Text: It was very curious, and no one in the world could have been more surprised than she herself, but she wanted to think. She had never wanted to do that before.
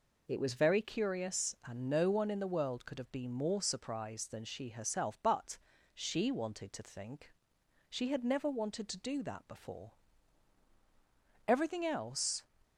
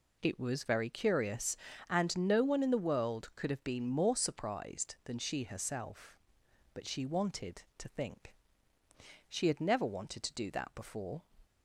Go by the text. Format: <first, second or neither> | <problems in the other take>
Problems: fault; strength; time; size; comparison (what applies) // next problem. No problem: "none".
second | pauses between "but" and "she"; at 5.5 s; 0.38 s long // goes on to say "Everything else"; noticeable; from 11.4 s on; 0.98 s long